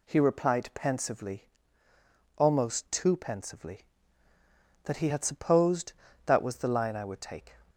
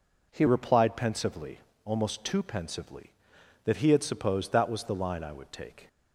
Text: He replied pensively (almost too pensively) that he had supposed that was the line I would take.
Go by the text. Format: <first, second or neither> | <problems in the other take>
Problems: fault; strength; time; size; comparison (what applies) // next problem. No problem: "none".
first | changes voice at "replied"; from 0.4 s on; 5.4 s long